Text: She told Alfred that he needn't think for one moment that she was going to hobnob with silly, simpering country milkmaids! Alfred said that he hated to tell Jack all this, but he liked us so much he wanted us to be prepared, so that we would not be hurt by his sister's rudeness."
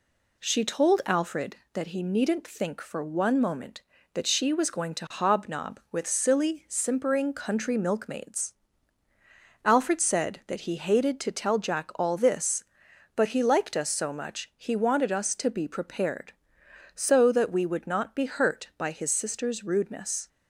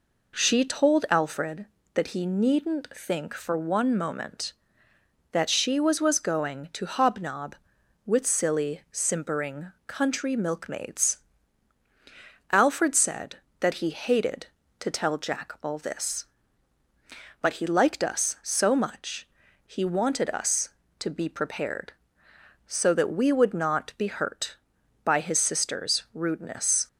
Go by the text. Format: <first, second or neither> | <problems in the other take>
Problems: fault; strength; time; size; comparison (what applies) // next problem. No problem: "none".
first | says "was" twice; at 6.0 s // pauses between "simpering" and "country"; slight; at 9.7 s; 0.16 s long // pauses between "much" and "he"; at 19.2 s; 0.40 s long